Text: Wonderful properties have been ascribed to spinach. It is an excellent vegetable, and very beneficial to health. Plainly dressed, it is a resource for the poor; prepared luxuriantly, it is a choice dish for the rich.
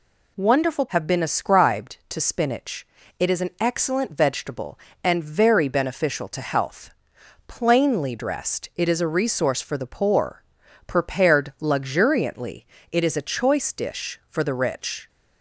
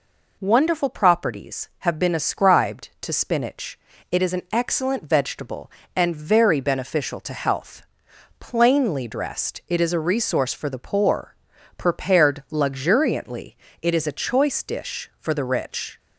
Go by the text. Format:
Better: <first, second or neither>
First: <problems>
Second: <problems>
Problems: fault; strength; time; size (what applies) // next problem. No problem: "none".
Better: second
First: skips "properties"; at 0.8 s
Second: none